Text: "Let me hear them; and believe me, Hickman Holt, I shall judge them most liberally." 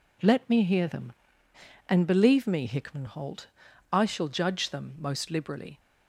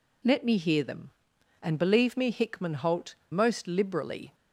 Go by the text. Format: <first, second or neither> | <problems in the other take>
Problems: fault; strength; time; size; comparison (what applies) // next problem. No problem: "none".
first | skips "I shall judge them"; at 3.2 s